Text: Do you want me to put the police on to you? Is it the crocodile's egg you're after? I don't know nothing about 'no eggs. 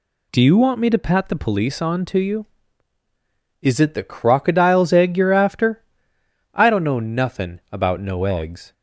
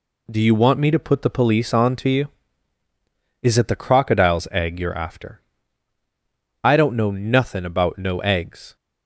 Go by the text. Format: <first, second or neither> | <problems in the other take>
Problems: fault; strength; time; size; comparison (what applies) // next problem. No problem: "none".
second | says "pat" for "put"; at 0.9 s